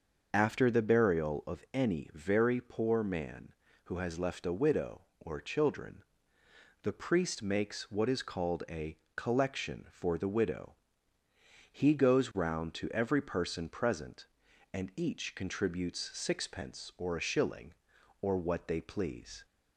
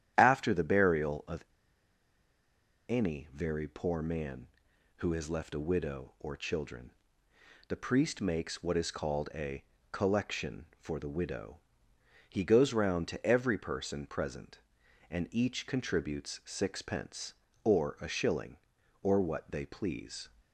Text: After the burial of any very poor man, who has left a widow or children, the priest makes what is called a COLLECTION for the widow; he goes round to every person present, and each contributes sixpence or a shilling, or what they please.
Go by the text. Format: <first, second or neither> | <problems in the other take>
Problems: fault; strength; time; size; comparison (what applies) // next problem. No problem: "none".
first | starts louder than the rest; strong; until 1.1 s; 10.5 dB; noticeable in the first // pauses between "of" and "any"; strong; at 1.4 s; 1.4 s long // pauses between "a" and "COLLECTION"; slight; at 9.6 s; 0.30 s long; slight in the first